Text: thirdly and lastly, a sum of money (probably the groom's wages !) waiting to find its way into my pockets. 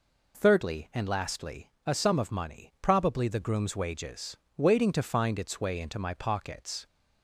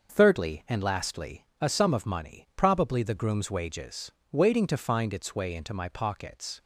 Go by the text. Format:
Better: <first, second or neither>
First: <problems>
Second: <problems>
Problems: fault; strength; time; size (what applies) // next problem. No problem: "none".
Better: first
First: none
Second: gets quieter; throughout; 6.5 dB